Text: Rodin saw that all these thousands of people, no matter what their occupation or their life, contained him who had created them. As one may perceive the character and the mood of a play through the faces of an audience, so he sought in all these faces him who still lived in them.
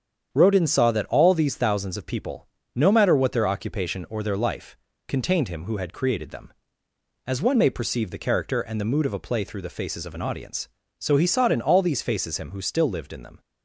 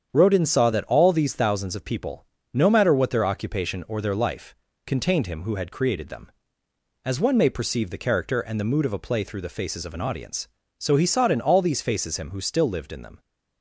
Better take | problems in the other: neither | starts louder than the rest; strong; the same in both

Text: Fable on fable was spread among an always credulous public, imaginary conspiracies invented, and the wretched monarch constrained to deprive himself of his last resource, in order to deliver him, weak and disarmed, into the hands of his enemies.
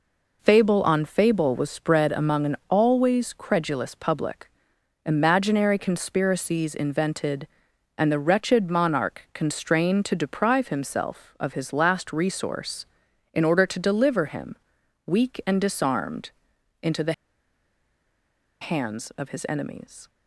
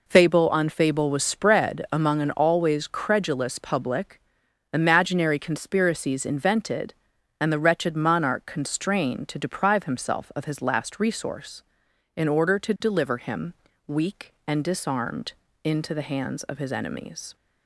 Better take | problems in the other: second | pauses between "the" and "hands"; strong; at 17.1 s; 1.4 s long

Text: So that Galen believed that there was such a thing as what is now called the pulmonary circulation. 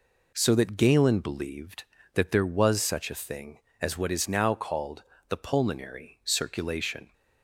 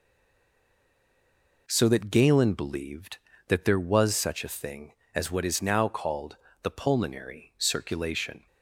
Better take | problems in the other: first | stays silent before the first word; noticeable; until 1.6 s; 1.6 s long // pauses between "called" and "the"; slight; at 6.3 s; 0.26 s long; slight in the first

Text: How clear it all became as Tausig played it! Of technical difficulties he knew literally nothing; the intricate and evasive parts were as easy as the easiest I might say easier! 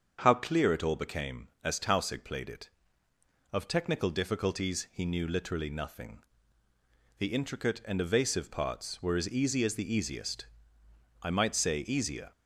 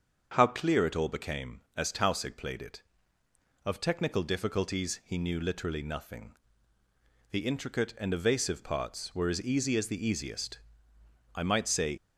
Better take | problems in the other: first | starts louder than the rest; until 1.3 s; 7 dB; also in the first // pauses between "easiest" and "I"; noticeable; at 10.6 s; 0.74 s long; noticeable in the first // stops before "easier"; at 11.9 s

